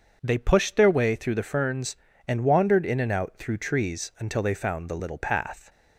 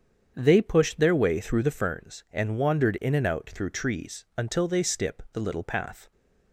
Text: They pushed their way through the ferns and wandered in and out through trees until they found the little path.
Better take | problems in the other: first | starts louder than the rest; strong; until 1.3 s; 7.5 dB; also in the first // says "stip" for "found"; at 4.8 s

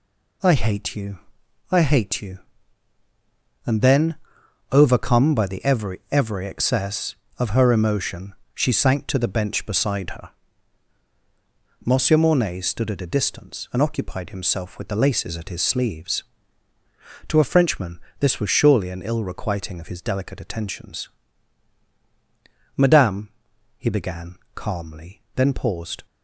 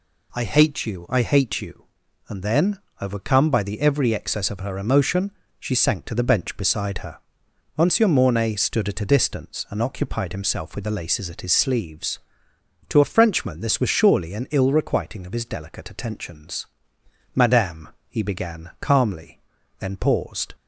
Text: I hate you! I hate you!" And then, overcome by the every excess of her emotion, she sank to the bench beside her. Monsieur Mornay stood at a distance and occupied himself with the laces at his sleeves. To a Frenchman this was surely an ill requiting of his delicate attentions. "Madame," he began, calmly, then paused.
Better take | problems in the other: second | says "every" twice; at 6.1 s // pauses between "Frenchman" and "this"; slight; at 17.9 s; 0.20 s long

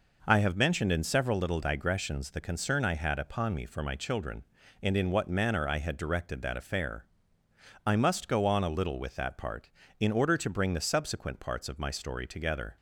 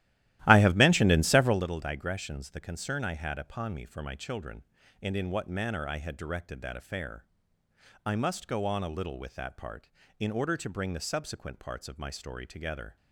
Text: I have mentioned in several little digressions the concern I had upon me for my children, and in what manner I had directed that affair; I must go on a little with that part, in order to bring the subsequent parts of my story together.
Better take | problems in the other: first | starts louder than the rest; strong; until 1.7 s; 14.5 dB

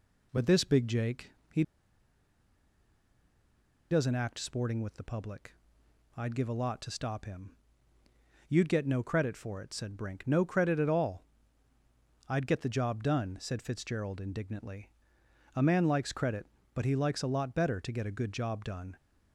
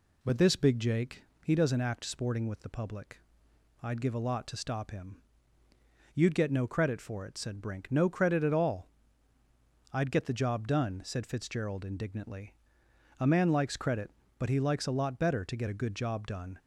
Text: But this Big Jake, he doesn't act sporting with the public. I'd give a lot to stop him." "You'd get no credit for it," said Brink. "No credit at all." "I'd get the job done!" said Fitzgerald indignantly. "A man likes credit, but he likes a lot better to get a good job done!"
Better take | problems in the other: second | pauses between "he" and "doesn't"; strong; at 1.6 s; 2.2 s long

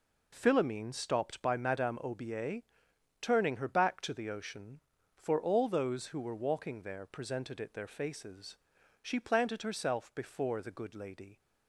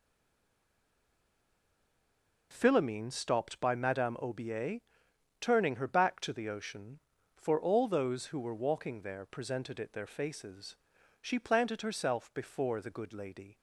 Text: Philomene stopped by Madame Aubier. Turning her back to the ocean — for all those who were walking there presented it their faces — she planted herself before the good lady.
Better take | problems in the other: first | stays silent before the first word; until 2.5 s; 2.5 s long

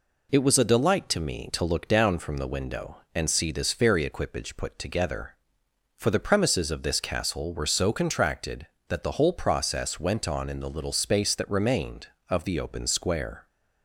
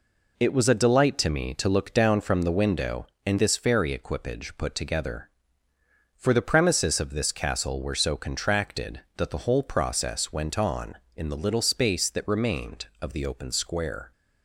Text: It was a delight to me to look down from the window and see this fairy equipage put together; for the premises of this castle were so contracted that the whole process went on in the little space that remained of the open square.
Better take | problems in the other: first | skips "see"; at 3.3 s

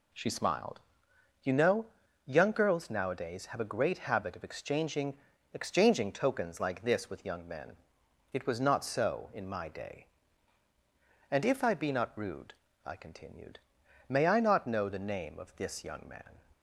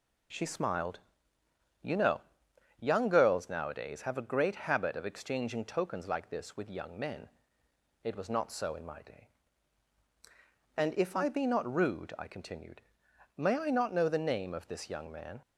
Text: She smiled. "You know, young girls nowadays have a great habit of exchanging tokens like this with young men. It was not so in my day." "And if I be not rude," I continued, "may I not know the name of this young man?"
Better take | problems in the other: second | says "exchanging" twice; at 5.5 s

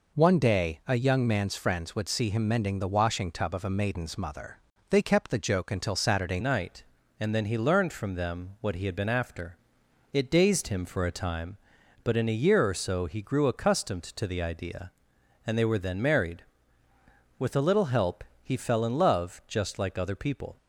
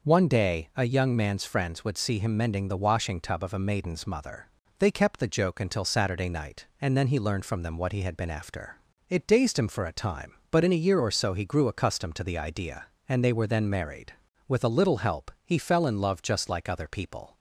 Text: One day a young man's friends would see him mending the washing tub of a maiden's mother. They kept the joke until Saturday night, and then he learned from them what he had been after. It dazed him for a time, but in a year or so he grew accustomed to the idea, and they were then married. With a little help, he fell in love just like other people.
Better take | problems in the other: second | changes voice at "night"; from 6.4 s on; 14.1 s long

